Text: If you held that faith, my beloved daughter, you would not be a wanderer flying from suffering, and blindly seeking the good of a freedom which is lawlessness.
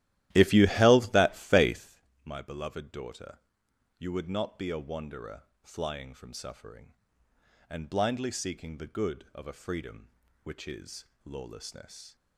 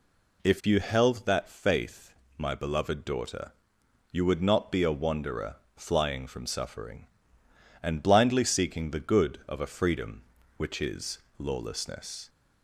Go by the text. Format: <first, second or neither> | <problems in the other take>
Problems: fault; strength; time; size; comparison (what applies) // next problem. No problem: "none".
second | starts louder than the rest; strong; until 2.0 s; 14 dB // pauses between "wanderer" and "flying"; slight; at 5.4 s; 0.22 s long; slight in the second // pauses between "is" and "lawlessness"; slight; at 11.0 s; 0.20 s long; slight in the second